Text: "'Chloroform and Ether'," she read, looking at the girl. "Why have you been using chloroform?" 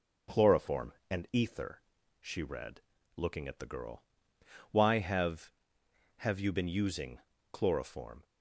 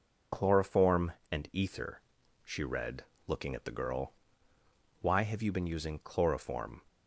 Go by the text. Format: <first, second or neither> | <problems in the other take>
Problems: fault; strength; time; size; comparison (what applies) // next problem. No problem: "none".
second | says "have" twice; at 6.1 s // pauses between "using" and "chloroform"; slight; at 7.1 s; 0.32 s long